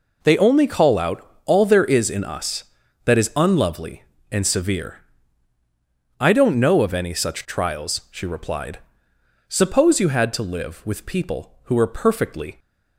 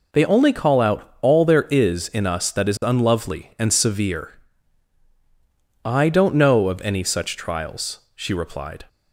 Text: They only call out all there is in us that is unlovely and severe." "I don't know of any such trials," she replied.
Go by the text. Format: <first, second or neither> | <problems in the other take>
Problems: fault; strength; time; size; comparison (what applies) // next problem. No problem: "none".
second | pauses between "out" and "all"; slight; at 1.2 s; 0.18 s long // goes on to say "Suppose you had to live with people who were perfectly"; strong; from 9.4 s on; 3.1 s long